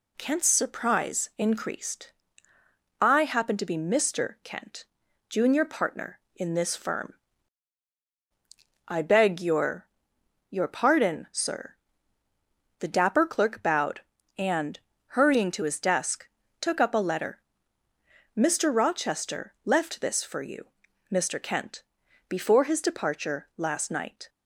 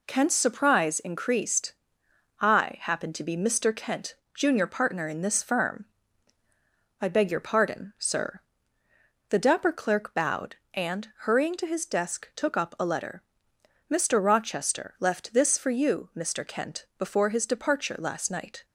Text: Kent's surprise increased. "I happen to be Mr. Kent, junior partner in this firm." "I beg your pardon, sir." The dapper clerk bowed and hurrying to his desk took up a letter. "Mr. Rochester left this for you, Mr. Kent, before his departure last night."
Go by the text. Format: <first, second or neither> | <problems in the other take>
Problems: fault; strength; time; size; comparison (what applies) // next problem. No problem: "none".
second | says "your" twice; at 10.5 s // pauses between "and" and "hurrying"; at 14.7 s; 0.38 s long // pauses between "desk" and "took"; slight; at 16.2 s; 0.34 s long